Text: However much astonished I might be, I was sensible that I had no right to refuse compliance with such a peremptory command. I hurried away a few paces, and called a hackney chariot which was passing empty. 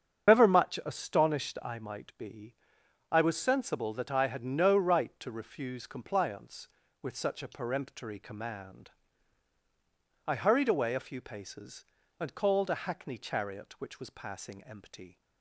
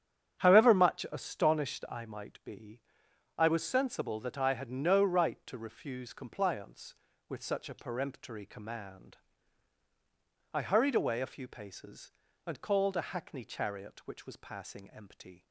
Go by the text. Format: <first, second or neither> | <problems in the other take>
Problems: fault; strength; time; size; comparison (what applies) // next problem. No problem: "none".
second | loses the start of "However"; at 0.2 s; 145 ms // starts louder than the rest; strong; until 1.3 s; 7.5 dB; strong in the second